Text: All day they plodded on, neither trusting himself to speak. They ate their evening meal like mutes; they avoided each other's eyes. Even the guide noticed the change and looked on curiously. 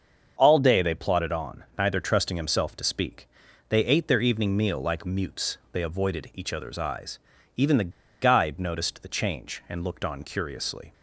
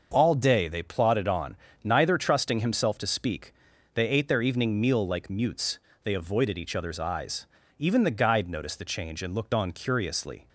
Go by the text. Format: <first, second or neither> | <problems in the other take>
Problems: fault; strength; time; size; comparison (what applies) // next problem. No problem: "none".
second | starts louder than the rest; until 1.3 s; 7 dB; noticeable in the second // pauses between "the" and "guide"; slight; at 7.9 s; 0.31 s long